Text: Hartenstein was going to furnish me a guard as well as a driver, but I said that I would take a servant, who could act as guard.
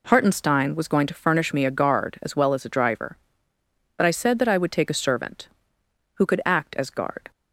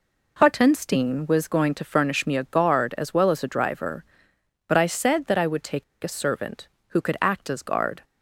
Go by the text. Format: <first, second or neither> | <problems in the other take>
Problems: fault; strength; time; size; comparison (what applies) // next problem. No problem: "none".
first | pauses between "take" and "a"; slight; at 5.8 s; 0.19 s long